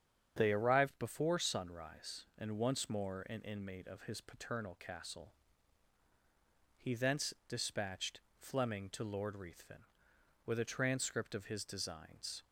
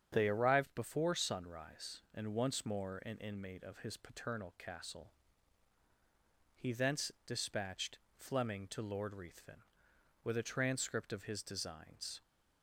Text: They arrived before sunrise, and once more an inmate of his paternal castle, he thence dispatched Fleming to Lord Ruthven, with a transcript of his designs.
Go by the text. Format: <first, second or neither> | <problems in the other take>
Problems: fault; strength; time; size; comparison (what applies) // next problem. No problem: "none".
neither | starts louder than the rest; strong; the same in both // pauses between "dispatched" and "Fleming"; slight; the same in both